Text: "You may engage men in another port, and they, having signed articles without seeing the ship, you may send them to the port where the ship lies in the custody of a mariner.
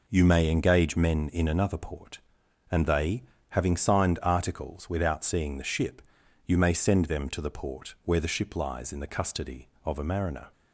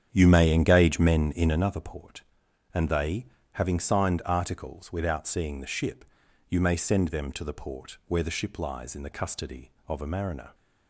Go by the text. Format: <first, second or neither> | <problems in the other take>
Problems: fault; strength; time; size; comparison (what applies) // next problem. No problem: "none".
first | starts louder than the rest; strong; until 1.7 s; 8.5 dB